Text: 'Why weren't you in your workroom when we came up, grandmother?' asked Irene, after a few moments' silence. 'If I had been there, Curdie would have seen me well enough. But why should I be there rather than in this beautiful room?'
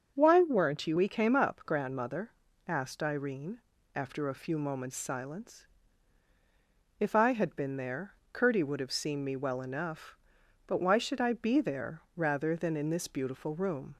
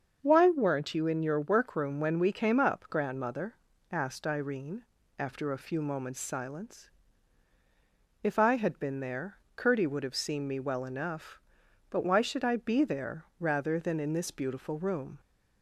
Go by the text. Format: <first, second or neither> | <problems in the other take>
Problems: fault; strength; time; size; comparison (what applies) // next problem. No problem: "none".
second | starts louder than the rest; until 1.1 s; 6 dB; also in the second // skips "in your workroom when"; at 0.9 s